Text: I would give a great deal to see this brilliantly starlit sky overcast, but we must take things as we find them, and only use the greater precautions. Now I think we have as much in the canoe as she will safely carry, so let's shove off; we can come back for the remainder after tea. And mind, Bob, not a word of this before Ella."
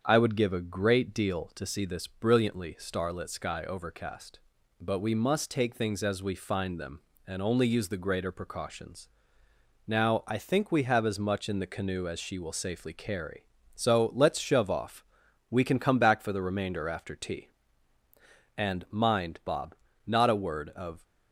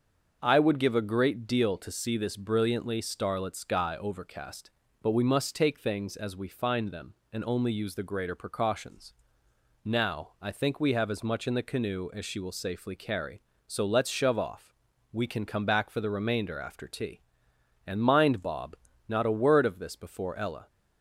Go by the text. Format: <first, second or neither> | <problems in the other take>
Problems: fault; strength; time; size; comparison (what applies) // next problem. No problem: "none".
second | starts louder than the rest; strong; until 1.0 s; 7.5 dB; also in the second // stops before "this before Ella"; at 21.0 s